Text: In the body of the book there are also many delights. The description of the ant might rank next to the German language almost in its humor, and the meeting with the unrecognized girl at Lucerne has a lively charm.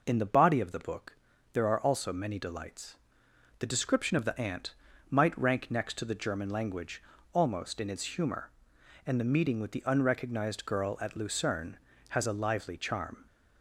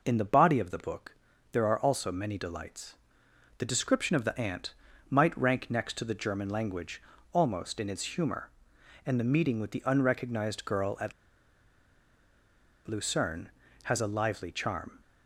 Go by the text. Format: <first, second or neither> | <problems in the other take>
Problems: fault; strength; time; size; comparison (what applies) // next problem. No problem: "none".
first | pauses between "book" and "there"; at 1.1 s; 0.38 s long; also in the first // pauses between "ant" and "might"; slight; at 4.7 s; 0.36 s long; slight in the first // pauses between "language" and "almost"; slight; at 6.9 s; 0.32 s long; slight in the first // pauses between "at" and "Lucerne"; strong; at 11.1 s; 1.7 s long